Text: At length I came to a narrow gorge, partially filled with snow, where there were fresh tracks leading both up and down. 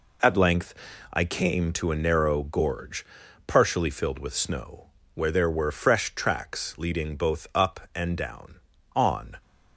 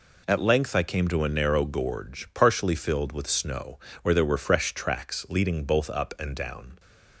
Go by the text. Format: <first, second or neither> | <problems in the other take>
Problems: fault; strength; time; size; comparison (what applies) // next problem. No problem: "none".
second | pauses between "length" and "I"; at 0.7 s; 0.38 s long // goes on to say "On"; slight; from 8.9 s on; 0.46 s long